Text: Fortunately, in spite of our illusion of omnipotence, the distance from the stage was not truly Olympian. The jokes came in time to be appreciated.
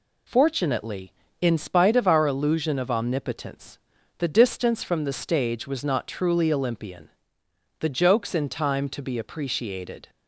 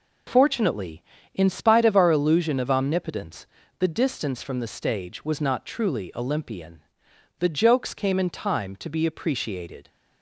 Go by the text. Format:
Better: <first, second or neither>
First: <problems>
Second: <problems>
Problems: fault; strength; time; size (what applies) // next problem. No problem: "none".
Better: second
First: skips "came"; at 8.3 s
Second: none